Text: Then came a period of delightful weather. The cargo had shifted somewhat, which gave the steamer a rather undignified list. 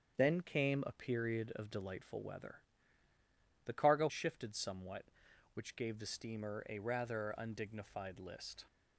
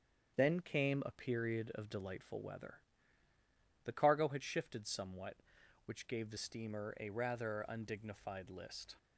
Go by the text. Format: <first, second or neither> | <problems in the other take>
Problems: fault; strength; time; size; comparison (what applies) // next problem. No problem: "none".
second | starts louder than the rest; strong; until 1.1 s; 7.5 dB; strong in the second // skips "had"; at 4.0 s